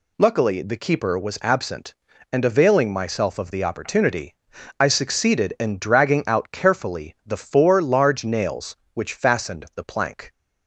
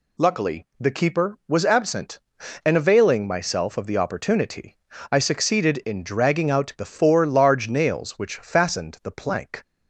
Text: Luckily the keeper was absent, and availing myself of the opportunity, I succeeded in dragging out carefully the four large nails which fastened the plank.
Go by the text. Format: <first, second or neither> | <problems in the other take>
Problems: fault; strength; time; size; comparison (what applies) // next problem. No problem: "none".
first | skips "carefully"; at 6.7 s